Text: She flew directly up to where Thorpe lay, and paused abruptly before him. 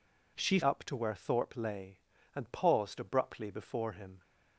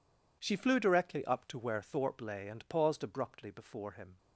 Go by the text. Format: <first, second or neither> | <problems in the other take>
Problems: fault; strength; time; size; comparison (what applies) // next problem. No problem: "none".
second | skips "flew directly"; at 0.6 s